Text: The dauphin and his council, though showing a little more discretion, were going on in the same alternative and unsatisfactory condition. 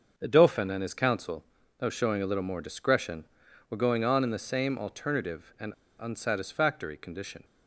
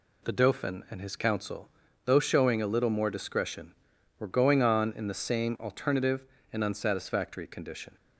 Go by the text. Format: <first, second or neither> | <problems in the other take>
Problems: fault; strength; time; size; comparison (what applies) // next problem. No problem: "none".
second | starts louder than the rest; until 1.1 s; 6.5 dB // pauses between "and" and "unsatisfactory"; slight; at 5.7 s; 0.24 s long